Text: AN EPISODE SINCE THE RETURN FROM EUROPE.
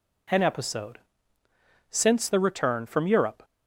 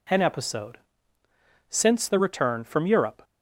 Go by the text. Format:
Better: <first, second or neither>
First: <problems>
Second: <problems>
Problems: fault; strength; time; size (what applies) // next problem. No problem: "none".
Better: neither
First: pauses between "EPISODE" and "SINCE"; noticeable; at 0.9 s; 0.90 s long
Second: pauses between "EPISODE" and "SINCE"; noticeable; at 0.7 s; 0.90 s long